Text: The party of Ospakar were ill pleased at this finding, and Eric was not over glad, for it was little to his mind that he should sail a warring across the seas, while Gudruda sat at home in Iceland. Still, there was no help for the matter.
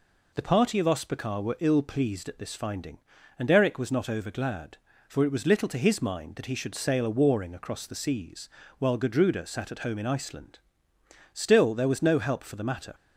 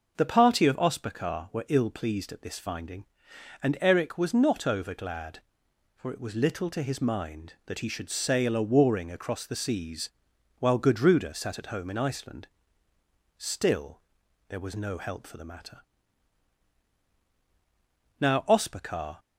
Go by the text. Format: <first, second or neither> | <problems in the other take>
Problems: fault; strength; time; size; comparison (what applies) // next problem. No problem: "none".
first | goes on to say "Now Ospakar"; noticeable; from 18.2 s on; 0.98 s long